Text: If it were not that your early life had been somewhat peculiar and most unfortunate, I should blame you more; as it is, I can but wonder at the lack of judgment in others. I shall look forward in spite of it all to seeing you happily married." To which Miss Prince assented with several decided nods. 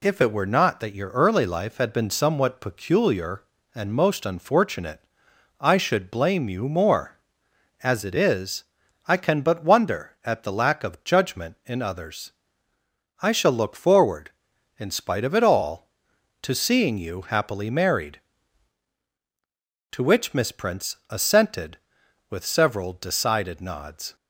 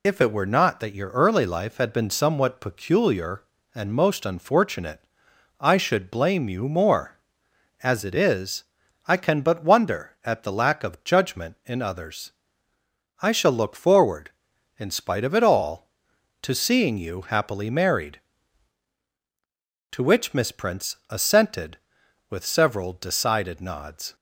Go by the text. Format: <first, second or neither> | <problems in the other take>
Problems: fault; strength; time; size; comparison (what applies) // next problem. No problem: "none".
first | loses the start of "If"; at 0.0 s; 30 ms